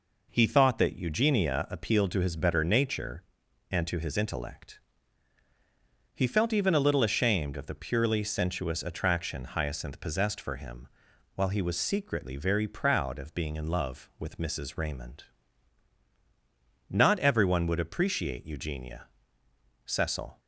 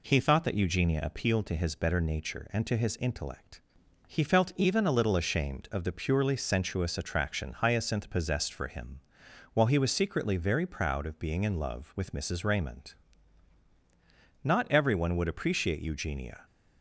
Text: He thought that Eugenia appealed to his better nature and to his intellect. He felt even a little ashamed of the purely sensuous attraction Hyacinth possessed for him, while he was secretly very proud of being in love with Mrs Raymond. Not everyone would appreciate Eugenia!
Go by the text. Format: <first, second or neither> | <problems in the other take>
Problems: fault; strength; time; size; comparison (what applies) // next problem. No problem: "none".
second | goes on to say "Cecil"; from 19.8 s on; 0.54 s long